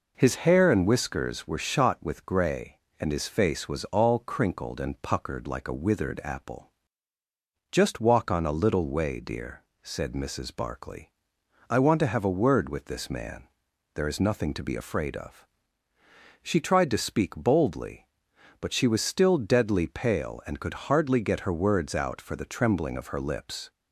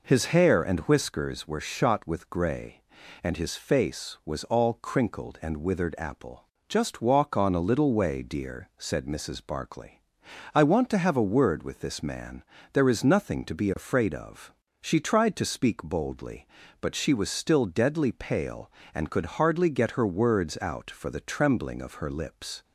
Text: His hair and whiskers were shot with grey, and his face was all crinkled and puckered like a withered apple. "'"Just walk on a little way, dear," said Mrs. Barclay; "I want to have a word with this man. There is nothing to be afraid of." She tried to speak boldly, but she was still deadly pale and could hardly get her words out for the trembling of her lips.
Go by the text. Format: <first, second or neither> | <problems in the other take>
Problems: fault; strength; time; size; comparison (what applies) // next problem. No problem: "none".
first | skips "puckered like a"; at 5.5 s